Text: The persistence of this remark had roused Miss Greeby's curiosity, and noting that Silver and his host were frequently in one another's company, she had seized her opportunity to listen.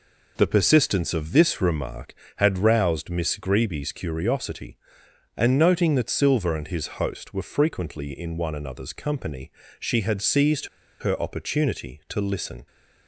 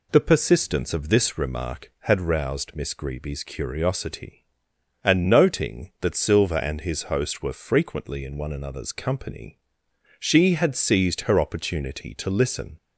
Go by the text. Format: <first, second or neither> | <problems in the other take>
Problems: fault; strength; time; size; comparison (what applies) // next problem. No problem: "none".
second | pauses between "seized" and "her"; slight; at 10.6 s; 0.33 s long